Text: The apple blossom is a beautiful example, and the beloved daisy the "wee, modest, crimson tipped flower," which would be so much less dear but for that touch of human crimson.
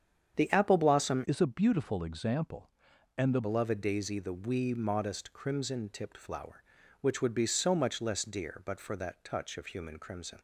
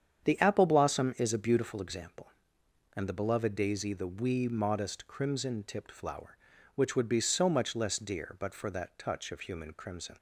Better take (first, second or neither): second